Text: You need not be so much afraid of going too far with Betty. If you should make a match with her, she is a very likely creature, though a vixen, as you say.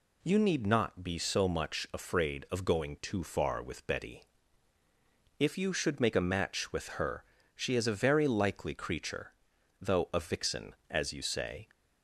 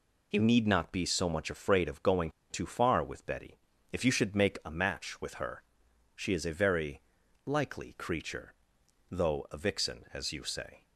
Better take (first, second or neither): first